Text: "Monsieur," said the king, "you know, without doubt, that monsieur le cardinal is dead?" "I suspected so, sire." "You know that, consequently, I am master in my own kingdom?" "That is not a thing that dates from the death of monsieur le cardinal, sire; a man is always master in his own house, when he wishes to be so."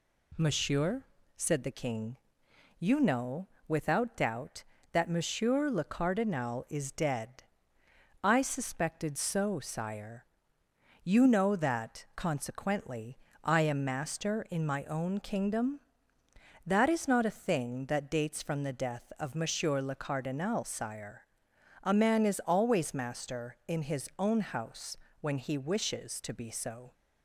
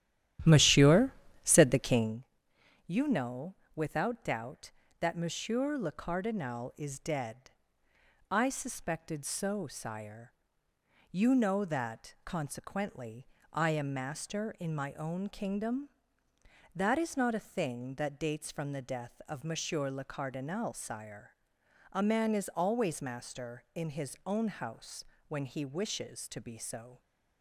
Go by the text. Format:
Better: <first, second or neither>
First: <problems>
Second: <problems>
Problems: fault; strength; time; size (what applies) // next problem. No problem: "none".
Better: first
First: none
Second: starts louder than the rest; strong; until 2.2 s; 12 dB